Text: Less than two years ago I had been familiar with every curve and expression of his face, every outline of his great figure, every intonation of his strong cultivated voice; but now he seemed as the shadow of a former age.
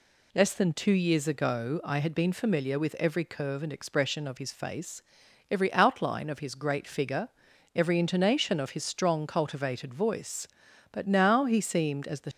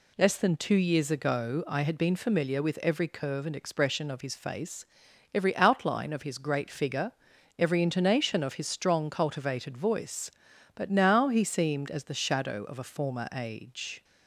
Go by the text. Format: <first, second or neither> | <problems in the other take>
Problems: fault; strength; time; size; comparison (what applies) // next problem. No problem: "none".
second | stops before "shadow of a former age"; at 12.3 s